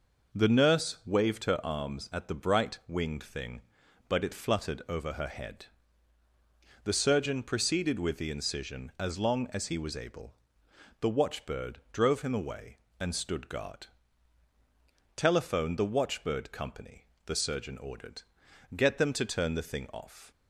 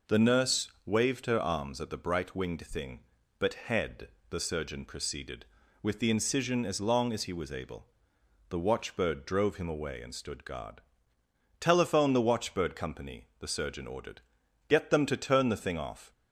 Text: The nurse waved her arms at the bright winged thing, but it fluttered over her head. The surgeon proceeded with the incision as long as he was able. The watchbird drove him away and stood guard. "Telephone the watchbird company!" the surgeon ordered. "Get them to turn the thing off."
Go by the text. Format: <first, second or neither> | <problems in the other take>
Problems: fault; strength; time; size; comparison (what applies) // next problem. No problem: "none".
first | skips "it fluttered over her"; at 3.5 s